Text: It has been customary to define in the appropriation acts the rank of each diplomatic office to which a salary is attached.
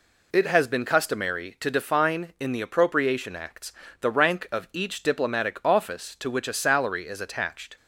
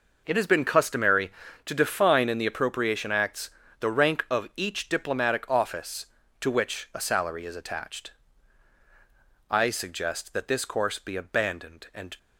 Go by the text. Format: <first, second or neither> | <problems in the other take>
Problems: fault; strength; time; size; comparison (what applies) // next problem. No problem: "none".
first | pauses between "acts" and "the"; slight; at 3.4 s; 0.30 s long; slight in the first // goes on to say "I suggest that this course be abandoned and"; strong; from 9.4 s on; 2.6 s long